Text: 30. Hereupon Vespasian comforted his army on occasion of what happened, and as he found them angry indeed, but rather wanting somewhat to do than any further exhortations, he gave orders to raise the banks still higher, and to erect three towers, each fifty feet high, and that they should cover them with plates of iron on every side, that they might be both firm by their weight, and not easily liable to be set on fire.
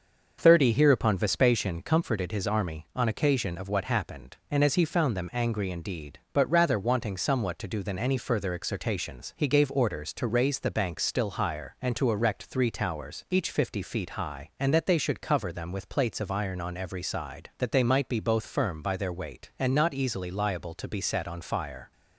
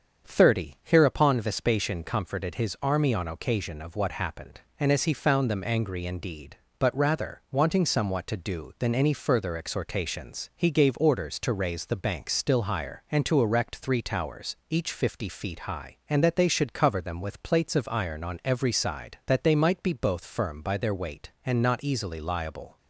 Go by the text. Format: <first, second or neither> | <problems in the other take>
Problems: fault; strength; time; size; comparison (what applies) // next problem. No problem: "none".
first | starts louder than the rest; strong; until 1.3 s; 7 dB; also in the first // stops before "to be set on fire"; at 22.7 s